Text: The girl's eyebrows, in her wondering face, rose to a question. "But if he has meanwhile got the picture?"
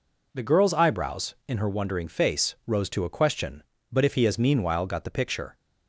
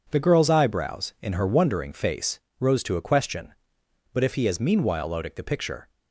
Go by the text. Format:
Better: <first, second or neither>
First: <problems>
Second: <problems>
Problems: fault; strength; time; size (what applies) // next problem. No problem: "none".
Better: first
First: none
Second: says "odic" for "got"; at 5.0 s